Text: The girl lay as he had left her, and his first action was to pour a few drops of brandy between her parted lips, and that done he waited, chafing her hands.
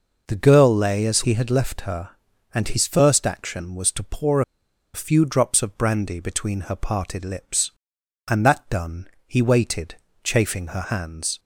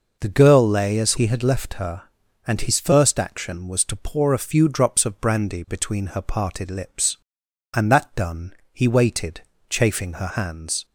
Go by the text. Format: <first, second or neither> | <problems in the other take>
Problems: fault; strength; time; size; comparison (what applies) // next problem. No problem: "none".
second | pauses between "pour" and "a"; noticeable; at 4.4 s; 0.52 s long // pauses between "done" and "he"; slight; at 9.0 s; 0.18 s long; slight in the second